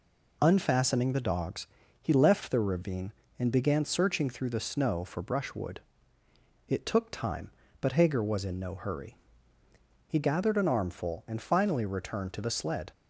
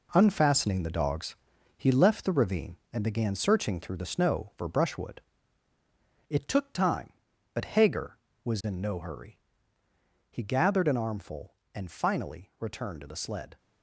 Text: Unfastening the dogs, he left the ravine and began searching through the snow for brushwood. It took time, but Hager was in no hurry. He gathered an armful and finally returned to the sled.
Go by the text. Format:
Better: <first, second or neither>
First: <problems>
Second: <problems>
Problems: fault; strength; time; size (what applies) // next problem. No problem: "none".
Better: first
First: none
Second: gets quieter; strong; throughout; 9 dB